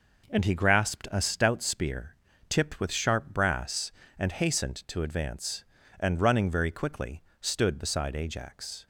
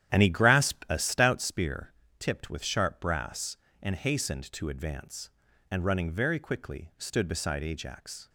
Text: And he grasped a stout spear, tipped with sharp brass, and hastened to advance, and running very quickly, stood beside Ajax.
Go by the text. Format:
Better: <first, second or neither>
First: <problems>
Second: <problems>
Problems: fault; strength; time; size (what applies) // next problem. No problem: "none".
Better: first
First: none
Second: starts louder than the rest; strong; until 1.5 s; 10.5 dB